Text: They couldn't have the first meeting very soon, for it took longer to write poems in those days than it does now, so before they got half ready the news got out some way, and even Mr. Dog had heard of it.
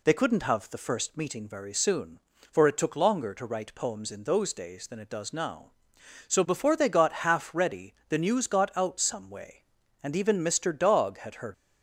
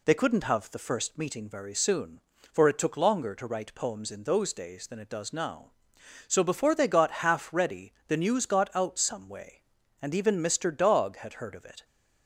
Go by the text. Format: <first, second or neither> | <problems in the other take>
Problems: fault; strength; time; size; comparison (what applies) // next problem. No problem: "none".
second | stops before "of it"; at 11.5 s